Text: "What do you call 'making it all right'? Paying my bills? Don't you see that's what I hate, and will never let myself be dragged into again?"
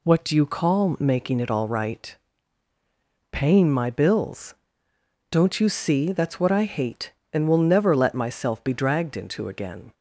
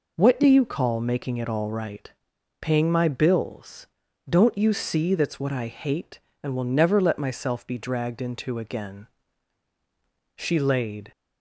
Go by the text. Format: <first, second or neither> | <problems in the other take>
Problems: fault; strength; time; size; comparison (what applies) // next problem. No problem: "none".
first | goes on to say "She laid"; noticeable; from 10.3 s on; 0.74 s long